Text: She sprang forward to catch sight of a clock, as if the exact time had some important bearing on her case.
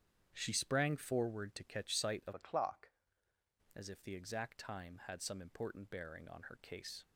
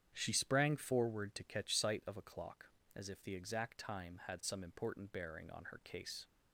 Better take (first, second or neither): second